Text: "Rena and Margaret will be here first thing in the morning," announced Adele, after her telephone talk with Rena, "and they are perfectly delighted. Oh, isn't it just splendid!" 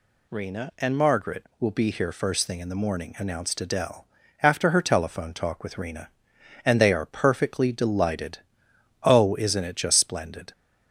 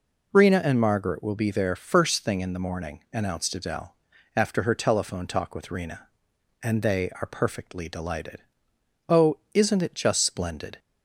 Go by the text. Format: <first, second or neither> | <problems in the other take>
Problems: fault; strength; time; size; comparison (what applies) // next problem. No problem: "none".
first | says "there" for "here"; at 1.5 s